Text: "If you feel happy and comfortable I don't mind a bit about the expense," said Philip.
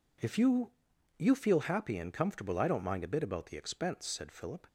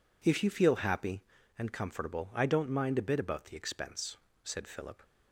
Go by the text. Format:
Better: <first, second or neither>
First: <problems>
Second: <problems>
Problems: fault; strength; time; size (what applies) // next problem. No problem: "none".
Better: second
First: says "you" twice; at 1.1 s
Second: none